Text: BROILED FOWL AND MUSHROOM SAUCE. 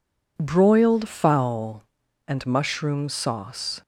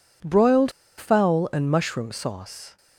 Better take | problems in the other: first | pauses between "BROILED" and "FOWL"; slight; at 0.6 s; 0.28 s long

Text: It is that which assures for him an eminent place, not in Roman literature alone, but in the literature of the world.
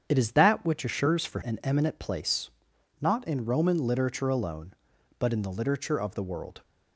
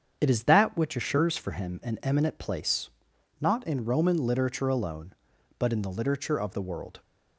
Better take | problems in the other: second | starts louder than the rest; strong; until 1.1 s; 8 dB; strong in the second // skips "him"; at 1.4 s

